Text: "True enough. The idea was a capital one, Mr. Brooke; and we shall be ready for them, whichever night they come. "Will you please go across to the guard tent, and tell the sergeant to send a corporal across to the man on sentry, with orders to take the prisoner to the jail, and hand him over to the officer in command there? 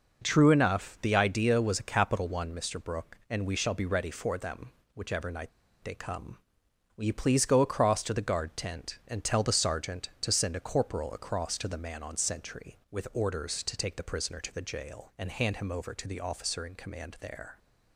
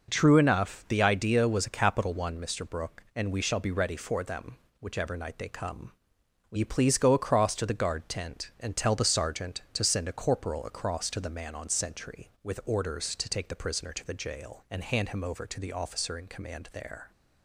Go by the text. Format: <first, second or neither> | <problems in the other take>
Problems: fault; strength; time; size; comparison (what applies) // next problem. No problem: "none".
second | pauses between "night" and "they"; slight; at 5.5 s; 0.33 s long